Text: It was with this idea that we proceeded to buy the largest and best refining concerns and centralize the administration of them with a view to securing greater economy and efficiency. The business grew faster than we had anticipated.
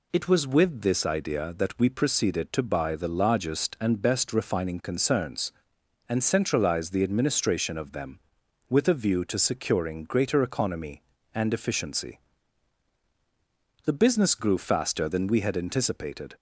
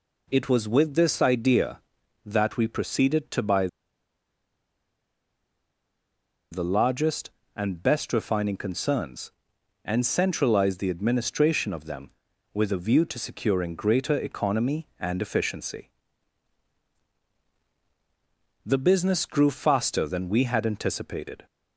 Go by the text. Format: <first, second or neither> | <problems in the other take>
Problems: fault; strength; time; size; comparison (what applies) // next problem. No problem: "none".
first | pauses between "buy" and "the"; strong; at 3.6 s; 2.8 s long